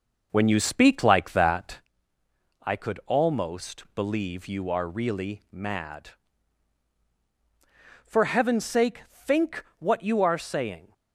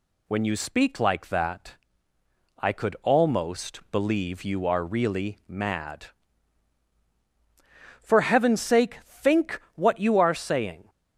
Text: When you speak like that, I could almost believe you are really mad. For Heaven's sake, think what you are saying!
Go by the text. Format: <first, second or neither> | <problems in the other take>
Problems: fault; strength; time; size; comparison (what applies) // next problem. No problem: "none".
second | starts louder than the rest; noticeable; until 1.9 s; 5.5 dB